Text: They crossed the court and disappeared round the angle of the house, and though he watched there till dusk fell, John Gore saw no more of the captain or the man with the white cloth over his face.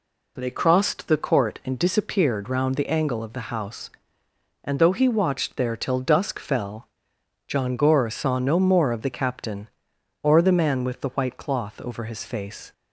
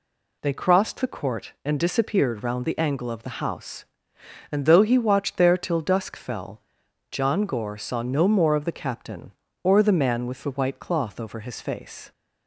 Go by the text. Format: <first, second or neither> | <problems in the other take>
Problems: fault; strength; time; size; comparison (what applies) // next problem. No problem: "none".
neither | none